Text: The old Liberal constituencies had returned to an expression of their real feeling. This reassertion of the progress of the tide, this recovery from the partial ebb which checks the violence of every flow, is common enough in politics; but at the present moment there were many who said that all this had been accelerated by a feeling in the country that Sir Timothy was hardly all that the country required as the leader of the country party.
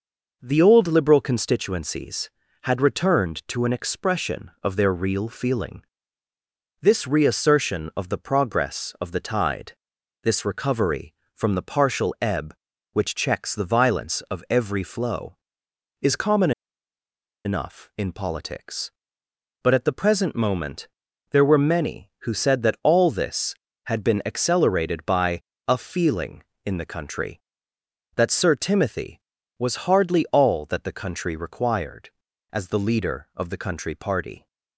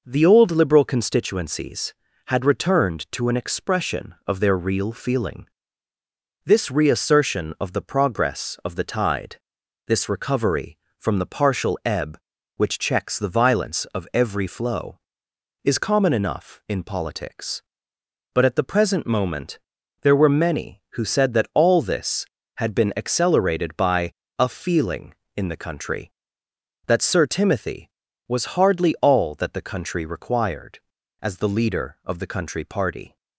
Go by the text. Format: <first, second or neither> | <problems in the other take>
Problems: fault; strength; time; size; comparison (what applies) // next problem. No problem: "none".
second | pauses between "common" and "enough"; noticeable; at 16.5 s; 0.93 s long // pauses between "moment" and "there"; at 20.8 s; 0.40 s long; also in the second // pauses between "by" and "a"; slight; at 25.4 s; 0.24 s long; slight in the second